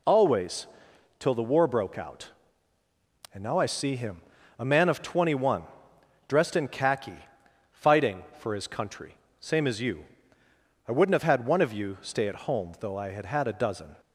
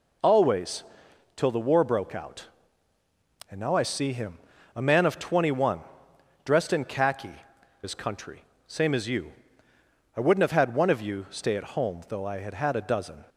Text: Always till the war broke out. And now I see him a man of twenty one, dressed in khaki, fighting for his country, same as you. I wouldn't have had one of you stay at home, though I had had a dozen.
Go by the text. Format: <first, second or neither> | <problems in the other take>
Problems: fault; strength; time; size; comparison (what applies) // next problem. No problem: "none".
first | pauses between "Always" and "till"; noticeable; at 0.8 s; 0.54 s long; noticeable in the first // pauses between "him" and "a"; slight; at 4.3 s; 0.36 s long; slight in the first // skips "fighting for"; at 7.5 s